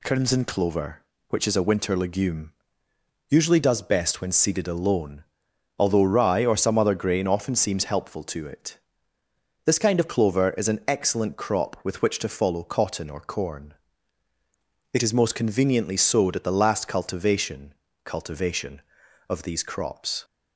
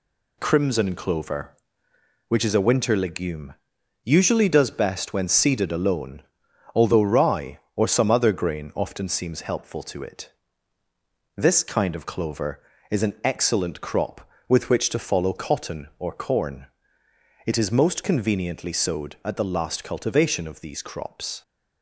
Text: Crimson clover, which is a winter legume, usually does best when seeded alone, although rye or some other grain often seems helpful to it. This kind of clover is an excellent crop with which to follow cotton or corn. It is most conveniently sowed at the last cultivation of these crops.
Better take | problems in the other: second | says "cultivation" twice; at 18.0 s

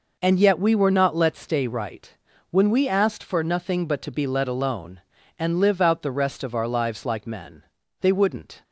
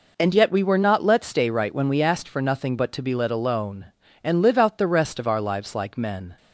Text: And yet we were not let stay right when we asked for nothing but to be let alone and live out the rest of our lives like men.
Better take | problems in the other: second | pauses between "right" and "when"; at 2.1 s; 0.38 s long // goes on to say "They wouldn't"; noticeable; from 7.9 s on; 0.64 s long

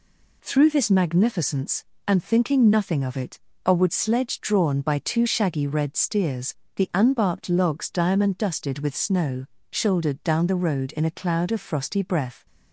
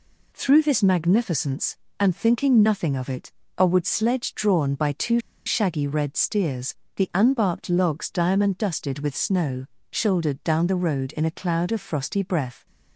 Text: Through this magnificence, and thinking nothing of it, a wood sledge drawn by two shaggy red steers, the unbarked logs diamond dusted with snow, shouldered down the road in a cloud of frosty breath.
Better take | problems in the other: first | pauses between "two" and "shaggy"; slight; at 5.2 s; 0.25 s long

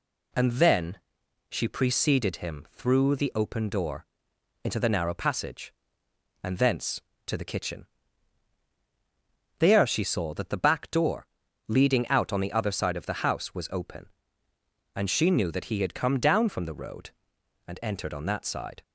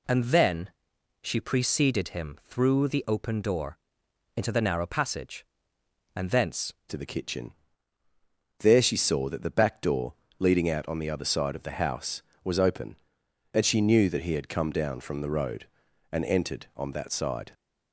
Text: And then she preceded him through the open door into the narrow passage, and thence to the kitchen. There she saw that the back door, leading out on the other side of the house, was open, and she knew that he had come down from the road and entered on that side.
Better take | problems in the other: first | pauses between "then" and "she"; noticeable; at 0.7 s; 0.52 s long; noticeable in the first // pauses between "door" and "into"; noticeable; at 3.7 s; 0.58 s long; noticeable in the first // changes voice at "to"; from 6.8 s on; 10.7 s long

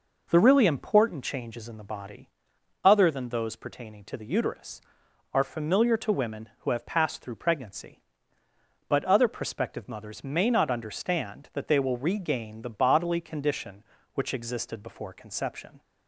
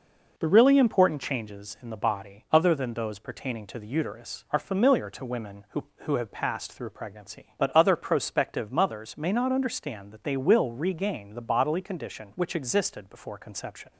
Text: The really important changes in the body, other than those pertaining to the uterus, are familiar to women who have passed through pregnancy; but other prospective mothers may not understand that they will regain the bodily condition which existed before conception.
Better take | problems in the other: first | says "who" twice; at 6.0 s

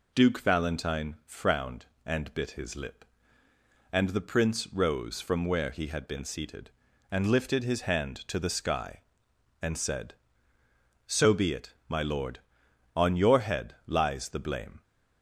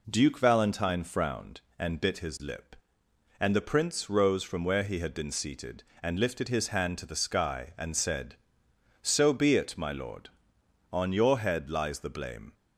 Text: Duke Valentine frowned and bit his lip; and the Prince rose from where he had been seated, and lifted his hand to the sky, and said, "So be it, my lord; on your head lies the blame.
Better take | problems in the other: neither | none

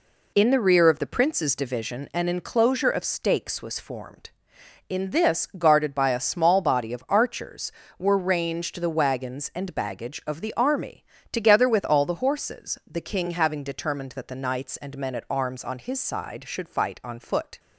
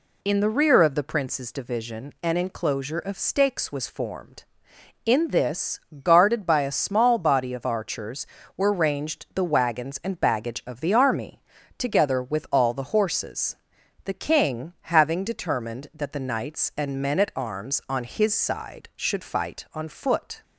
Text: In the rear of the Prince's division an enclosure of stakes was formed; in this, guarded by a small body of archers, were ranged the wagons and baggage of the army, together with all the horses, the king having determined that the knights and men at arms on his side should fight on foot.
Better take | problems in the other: neither | none

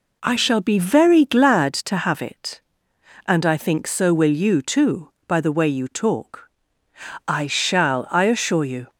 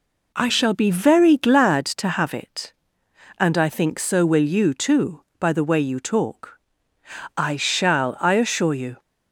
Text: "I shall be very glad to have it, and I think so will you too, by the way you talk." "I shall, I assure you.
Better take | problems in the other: neither | none

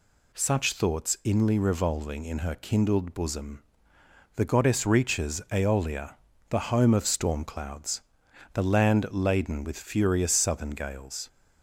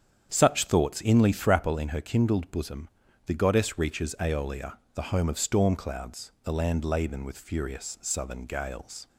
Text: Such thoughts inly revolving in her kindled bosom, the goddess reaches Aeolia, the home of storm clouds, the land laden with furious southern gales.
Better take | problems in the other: first | starts louder than the rest; strong; until 1.3 s; 8.5 dB // says "thrapple" for "revolving"; at 1.3 s

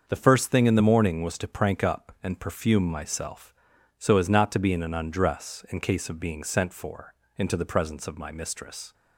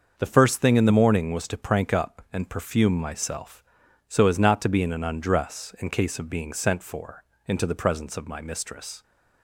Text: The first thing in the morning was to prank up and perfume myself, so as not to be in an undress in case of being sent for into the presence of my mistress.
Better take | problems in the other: neither | starts louder than the rest; the same in both // pauses between "for" and "into"; slight; the same in both

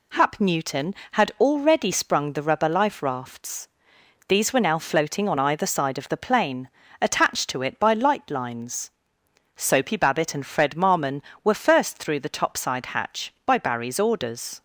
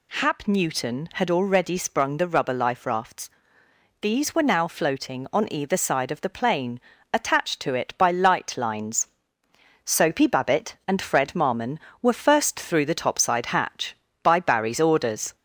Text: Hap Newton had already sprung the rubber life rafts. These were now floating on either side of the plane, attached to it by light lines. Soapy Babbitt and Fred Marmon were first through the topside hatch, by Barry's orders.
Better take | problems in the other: first | gets louder; slight; throughout; 2 dB

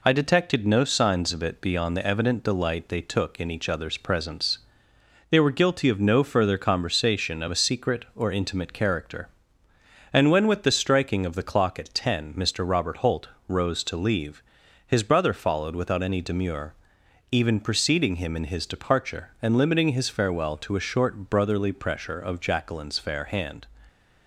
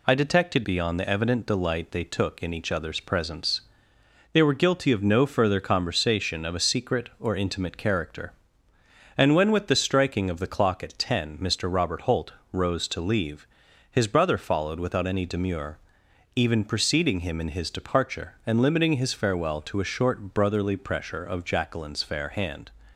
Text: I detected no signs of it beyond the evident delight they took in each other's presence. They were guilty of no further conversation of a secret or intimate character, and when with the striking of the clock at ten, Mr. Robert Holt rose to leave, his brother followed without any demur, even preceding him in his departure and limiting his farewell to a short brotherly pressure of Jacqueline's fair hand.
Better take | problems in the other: first | skips "no signs of it"; at 0.6 s // pauses between "Holt" and "rose"; slight; at 12.3 s; 0.18 s long; slight in the first

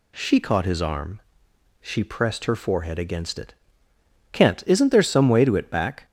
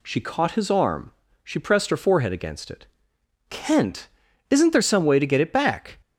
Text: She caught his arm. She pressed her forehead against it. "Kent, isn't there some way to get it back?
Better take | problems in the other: second | skips "get"; at 5.5 s

